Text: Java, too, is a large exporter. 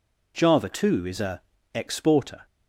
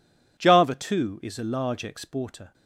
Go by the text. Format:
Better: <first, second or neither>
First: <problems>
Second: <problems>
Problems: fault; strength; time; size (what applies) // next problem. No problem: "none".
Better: second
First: skips "large"; at 1.5 s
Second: none